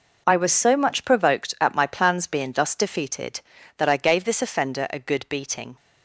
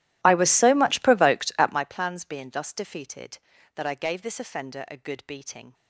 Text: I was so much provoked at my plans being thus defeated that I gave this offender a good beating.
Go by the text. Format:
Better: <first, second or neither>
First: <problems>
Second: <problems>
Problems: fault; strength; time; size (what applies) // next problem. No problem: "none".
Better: first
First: none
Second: starts louder than the rest; strong; until 1.9 s; 14.5 dB